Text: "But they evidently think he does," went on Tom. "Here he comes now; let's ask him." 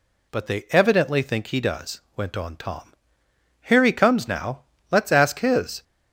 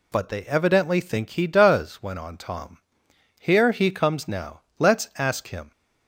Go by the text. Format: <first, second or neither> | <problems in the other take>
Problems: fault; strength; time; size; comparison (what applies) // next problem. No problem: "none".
second | says "his" for "him"; at 5.3 s